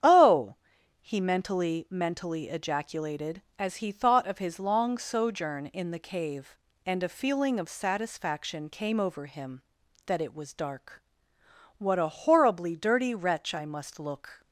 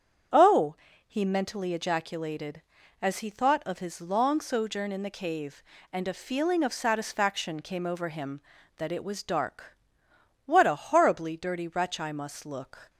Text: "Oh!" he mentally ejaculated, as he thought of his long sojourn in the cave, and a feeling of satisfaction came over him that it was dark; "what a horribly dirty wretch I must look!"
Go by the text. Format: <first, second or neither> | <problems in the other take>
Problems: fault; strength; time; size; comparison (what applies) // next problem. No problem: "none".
second | starts louder than the rest; strong; until 1.4 s; 9 dB; strong in the second // says "mentally" twice; at 1.8 s